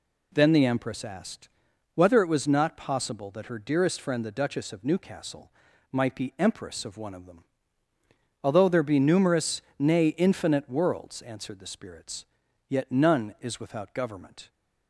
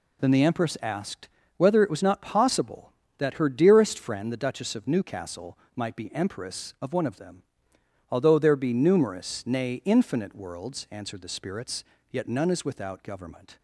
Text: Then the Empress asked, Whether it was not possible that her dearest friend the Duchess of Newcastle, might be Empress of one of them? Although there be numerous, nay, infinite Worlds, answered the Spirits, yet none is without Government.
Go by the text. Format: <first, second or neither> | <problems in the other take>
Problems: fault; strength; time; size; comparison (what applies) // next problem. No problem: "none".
neither | none